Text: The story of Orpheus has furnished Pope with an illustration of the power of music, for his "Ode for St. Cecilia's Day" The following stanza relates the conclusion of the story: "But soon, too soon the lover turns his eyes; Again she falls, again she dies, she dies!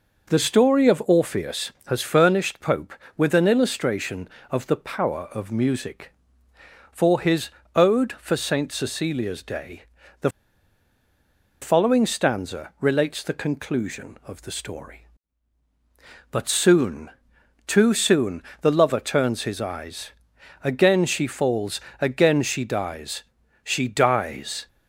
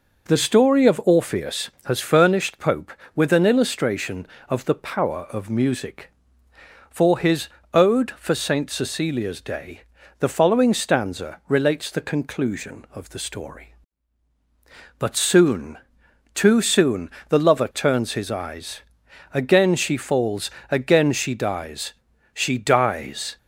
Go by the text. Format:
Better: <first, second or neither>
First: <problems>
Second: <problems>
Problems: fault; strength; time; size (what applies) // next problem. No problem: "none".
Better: second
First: pauses between "his" and "Ode"; slight; at 7.4 s; 0.26 s long // pauses between "Day" and "The"; slight; at 9.8 s; 0.36 s long // pauses between "The" and "following"; strong; at 10.2 s; 1.3 s long // pauses between "soon" and "the"; slight; at 18.4 s; 0.20 s long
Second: pauses between "his" and "Ode"; slight; at 7.4 s; 0.26 s long // pauses between "Day" and "The"; slight; at 9.8 s; 0.36 s long // pauses between "soon" and "the"; slight; at 17.0 s; 0.20 s long